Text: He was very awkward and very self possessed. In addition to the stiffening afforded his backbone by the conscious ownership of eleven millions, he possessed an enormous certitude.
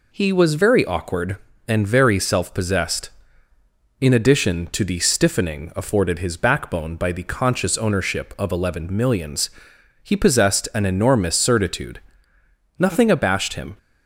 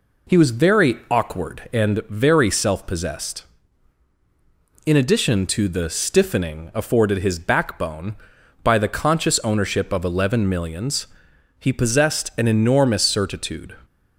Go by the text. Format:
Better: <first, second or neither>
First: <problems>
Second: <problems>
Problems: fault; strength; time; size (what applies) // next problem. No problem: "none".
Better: second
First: goes on to say "Nothing abashed him"; noticeable; from 12.7 s on; 1.0 s long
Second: none